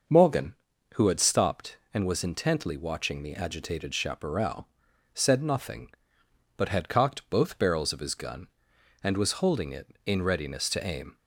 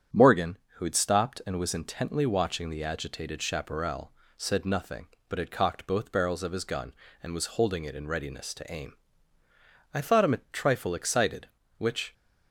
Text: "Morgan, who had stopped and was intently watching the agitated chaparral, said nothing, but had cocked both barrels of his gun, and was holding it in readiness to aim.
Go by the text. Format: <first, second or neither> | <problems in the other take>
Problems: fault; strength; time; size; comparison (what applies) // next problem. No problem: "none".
first | starts louder than the rest; strong; until 1.3 s; 8.5 dB; also in the first // goes on to say "I thought him a trifle excited which"; strong; from 9.9 s on; 2.2 s long